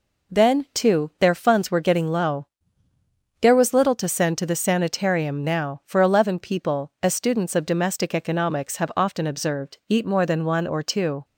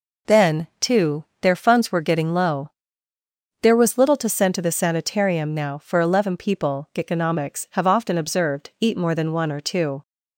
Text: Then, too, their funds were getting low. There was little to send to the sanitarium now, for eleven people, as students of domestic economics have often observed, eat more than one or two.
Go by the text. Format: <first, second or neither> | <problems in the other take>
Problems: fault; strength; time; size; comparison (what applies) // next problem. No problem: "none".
first | skips "as students of domestic"; at 6.9 s